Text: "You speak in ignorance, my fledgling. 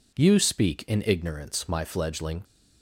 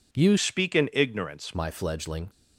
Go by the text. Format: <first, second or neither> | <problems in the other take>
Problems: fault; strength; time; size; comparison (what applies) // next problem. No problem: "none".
first | changes voice from "speak" to "ignorance"; from 0.3 to 1.5 s; 1.2 s long